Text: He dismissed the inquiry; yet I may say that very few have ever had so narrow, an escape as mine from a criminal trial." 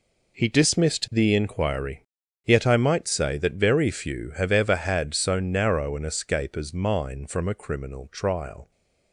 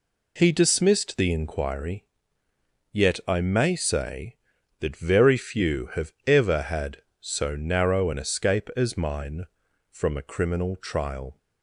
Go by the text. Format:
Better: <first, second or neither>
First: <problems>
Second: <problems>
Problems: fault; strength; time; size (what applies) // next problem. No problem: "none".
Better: second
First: says "might" for "may"; at 2.7 s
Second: none